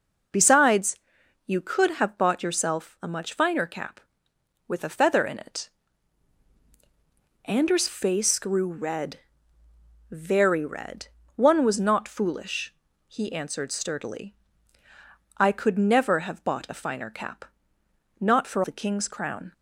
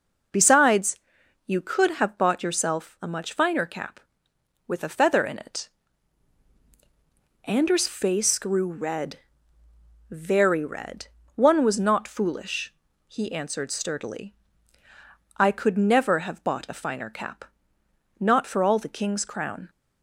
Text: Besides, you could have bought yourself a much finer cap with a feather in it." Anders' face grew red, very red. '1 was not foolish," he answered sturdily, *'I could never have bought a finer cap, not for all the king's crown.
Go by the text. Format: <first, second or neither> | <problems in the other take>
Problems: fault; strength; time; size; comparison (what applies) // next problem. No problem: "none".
second | skips "all"; at 18.6 s